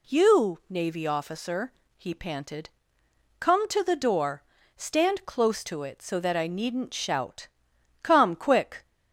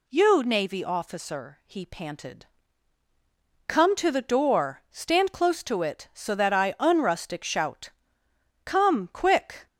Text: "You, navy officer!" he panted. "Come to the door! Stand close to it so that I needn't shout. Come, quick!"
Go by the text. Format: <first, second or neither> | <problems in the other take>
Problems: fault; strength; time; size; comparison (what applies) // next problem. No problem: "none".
first | says "unrustic" for "needn't"; at 6.7 s